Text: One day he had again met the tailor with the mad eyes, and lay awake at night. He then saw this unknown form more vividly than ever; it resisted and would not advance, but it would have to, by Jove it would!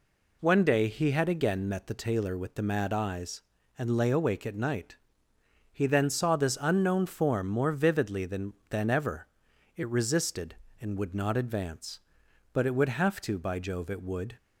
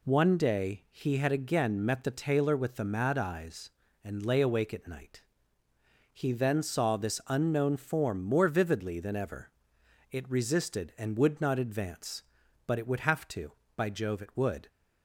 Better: second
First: says "than" twice; at 8.6 s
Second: none

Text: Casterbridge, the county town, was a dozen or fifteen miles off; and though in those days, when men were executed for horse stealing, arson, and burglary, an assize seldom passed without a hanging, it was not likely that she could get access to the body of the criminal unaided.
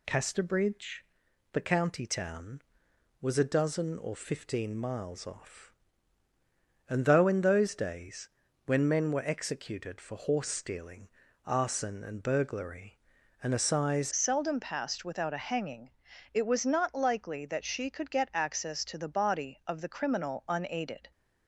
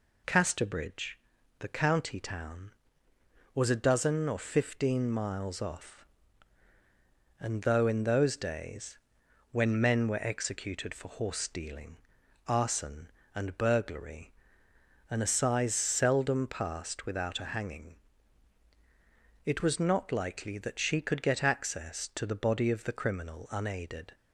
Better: second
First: changes voice at "seldom"; from 14.1 s on; 7.0 s long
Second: none

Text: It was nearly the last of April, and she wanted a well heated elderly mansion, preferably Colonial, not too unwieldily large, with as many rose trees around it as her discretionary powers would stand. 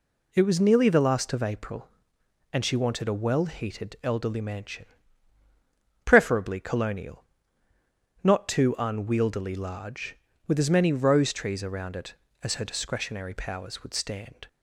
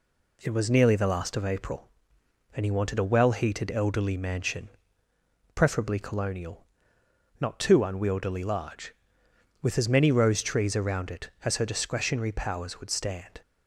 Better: first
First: none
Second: says "he" for "she"; at 2.6 s

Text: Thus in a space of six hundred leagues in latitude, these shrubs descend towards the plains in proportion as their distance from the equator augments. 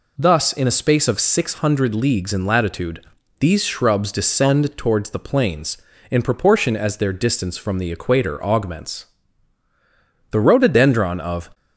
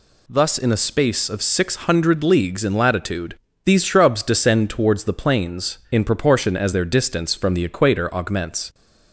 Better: second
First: goes on to say "The rhododendron of"; noticeable; from 10.3 s on; 1.2 s long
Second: none

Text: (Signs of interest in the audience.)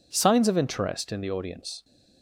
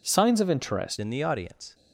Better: first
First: none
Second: changes voice at "in"; from 0.9 s on; 0.8 s long

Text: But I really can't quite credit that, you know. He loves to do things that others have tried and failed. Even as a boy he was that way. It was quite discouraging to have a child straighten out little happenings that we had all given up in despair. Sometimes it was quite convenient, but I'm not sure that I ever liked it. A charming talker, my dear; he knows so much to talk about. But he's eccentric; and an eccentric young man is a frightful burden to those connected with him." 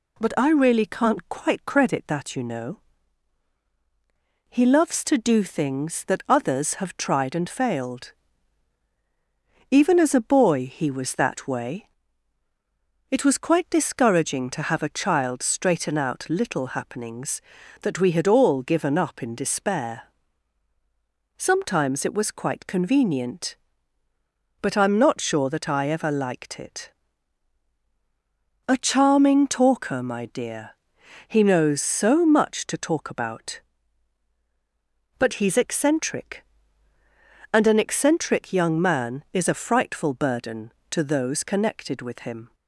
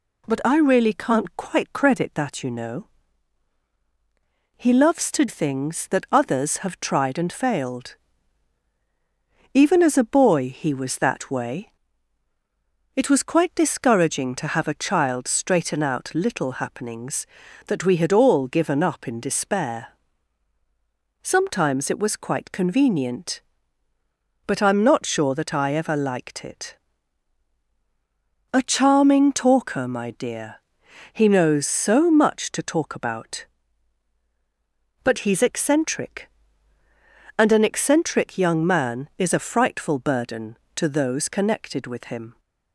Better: first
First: none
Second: skips "do"; at 5.2 s

